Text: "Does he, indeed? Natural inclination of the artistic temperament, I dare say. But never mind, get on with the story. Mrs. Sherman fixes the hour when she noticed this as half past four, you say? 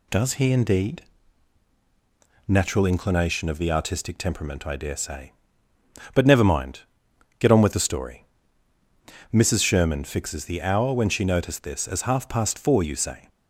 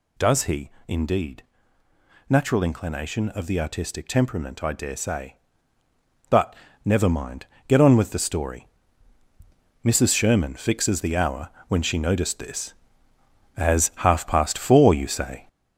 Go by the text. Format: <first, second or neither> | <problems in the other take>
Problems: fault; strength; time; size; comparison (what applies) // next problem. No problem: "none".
first | gets louder; noticeable; throughout; 6 dB // pauses between "But" and "never"; slight; at 6.5 s; 0.28 s long // pauses between "hour" and "when"; slight; at 11.4 s; 0.18 s long